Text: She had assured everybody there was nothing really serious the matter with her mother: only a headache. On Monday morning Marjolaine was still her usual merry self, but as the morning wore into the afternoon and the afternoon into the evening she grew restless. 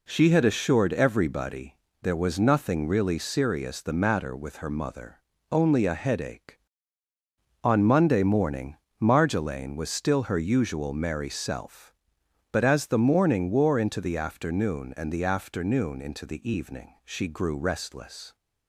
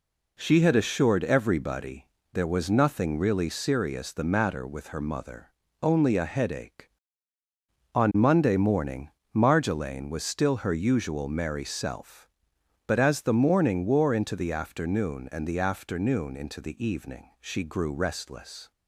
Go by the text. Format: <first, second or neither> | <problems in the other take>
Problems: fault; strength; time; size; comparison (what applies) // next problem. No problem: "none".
neither | pauses between "everybody" and "there"; slight; the same in both // pauses between "morning" and "Marjolaine"; slight; the same in both